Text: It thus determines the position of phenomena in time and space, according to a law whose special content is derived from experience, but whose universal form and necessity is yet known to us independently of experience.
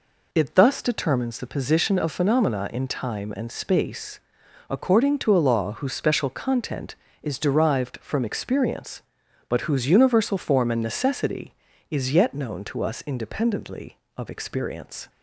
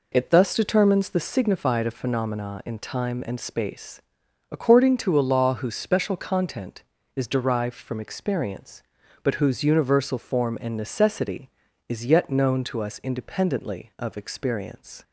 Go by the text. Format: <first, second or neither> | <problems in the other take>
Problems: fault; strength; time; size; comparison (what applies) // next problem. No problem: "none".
first | says "signified" for "position"; at 1.1 s